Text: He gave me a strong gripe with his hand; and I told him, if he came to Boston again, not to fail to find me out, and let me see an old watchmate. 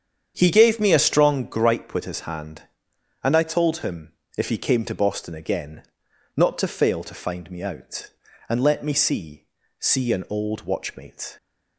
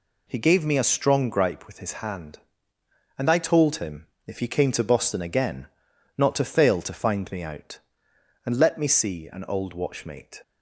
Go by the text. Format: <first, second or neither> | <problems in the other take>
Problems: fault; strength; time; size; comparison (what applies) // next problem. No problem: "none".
second | starts louder than the rest; strong; until 1.3 s; 8 dB // says "see" twice; at 9.7 s